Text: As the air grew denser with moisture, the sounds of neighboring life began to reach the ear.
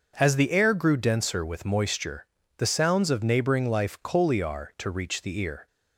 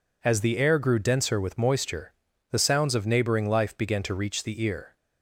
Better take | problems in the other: second | starts louder than the rest; noticeable; until 1.1 s; 6 dB // says "coliar" for "began"; at 4.0 s

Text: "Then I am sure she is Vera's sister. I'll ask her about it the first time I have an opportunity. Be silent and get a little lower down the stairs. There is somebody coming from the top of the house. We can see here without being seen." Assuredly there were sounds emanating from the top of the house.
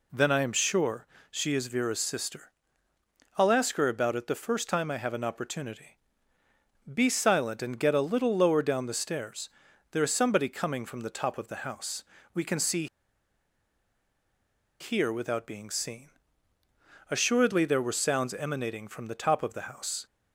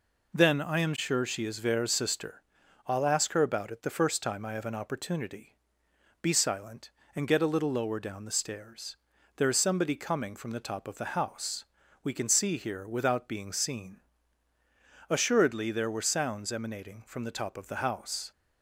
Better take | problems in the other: second | pauses between "sure" and "she"; slight; at 1.0 s; 0.24 s long // pauses between "see" and "here"; strong; at 12.8 s; 1.9 s long

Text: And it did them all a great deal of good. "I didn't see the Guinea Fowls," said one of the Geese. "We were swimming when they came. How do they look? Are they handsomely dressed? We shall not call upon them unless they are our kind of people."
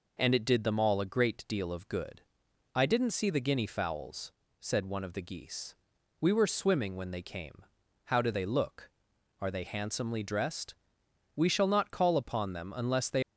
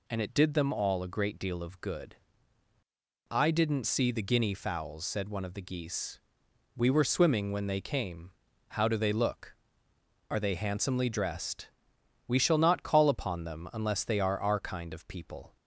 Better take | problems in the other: second | stops before "are our kind of people"; at 13.2 s

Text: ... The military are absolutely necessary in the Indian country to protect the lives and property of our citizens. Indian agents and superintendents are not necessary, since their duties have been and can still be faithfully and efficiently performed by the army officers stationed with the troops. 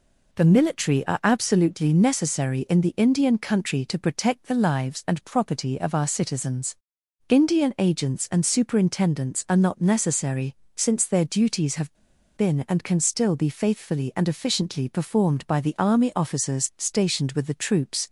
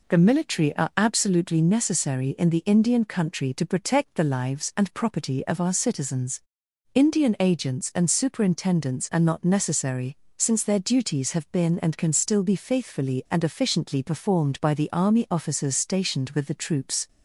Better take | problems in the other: second | pauses between "have" and "been"; at 11.9 s; 0.43 s long

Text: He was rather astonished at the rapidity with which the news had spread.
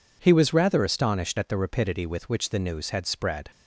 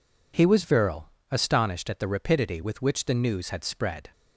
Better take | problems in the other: first | says "virile" for "rather"; at 0.6 s

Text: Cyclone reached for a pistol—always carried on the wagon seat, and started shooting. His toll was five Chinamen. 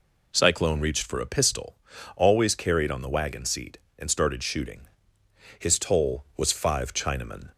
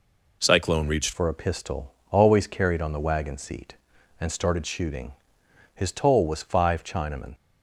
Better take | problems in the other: first | changes voice at "for"; from 1.1 s on; 6.2 s long

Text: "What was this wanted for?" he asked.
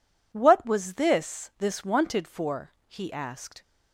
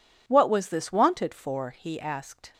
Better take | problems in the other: second | says "this" twice; at 1.5 s

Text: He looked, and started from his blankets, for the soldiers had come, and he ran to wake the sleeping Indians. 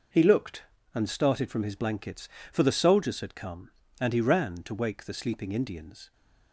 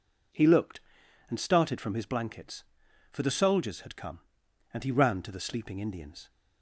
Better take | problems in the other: first | skips "wake"; at 5.3 s

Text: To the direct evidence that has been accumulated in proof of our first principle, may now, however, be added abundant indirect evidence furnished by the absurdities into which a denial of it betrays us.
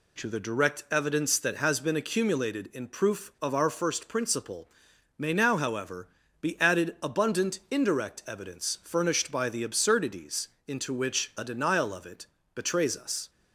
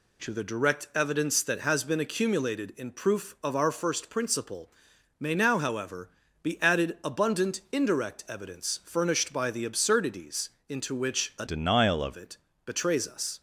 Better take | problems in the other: first | pauses between "absurdities" and "into"; slight; at 10.5 s; 0.18 s long; slight in the first // changes voice from "denial" to "of"; from 11.4 to 12.1 s; 0.7 s long // pauses between "it" and "betrays"; slight; at 12.3 s; 0.28 s long; slight in the first

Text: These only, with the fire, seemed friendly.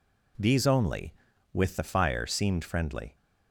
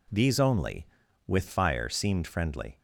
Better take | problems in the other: first | skips "the"; at 1.4 s

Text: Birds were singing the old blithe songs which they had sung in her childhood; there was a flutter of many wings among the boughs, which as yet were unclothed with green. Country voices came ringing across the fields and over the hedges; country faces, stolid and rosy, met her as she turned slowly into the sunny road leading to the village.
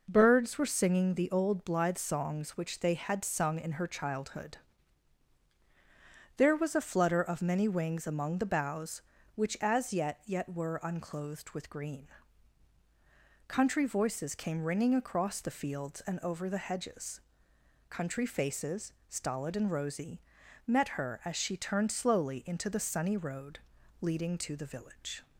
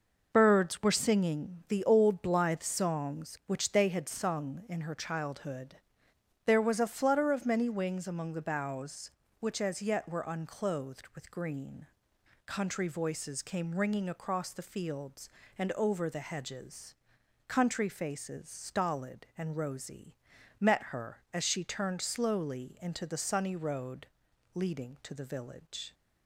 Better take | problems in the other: second | says "yet" twice; at 10.2 s // pauses between "road" and "leading"; at 23.6 s; 0.42 s long; noticeable in the second

